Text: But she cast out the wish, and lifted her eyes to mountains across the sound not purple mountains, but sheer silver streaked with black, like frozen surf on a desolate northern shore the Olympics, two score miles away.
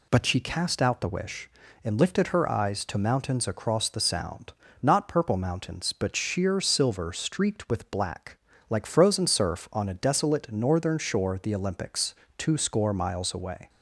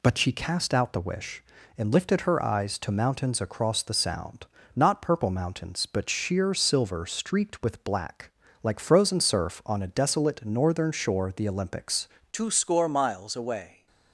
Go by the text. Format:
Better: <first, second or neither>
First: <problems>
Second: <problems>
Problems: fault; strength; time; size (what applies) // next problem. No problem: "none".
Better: first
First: pauses between "sound" and "not"; slight; at 4.5 s; 0.30 s long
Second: pauses between "sound" and "not"; slight; at 4.4 s; 0.30 s long // changes voice at "two"; from 12.3 s on; 1.5 s long